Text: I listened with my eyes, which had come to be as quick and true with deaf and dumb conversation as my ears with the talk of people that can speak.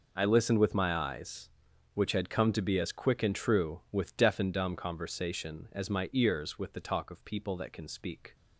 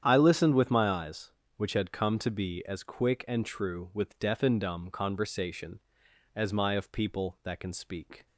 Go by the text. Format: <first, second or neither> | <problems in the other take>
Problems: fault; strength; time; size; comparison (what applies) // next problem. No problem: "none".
first | starts louder than the rest; strong; until 1.0 s; 9 dB // skips "ears with the talk"; at 6.7 s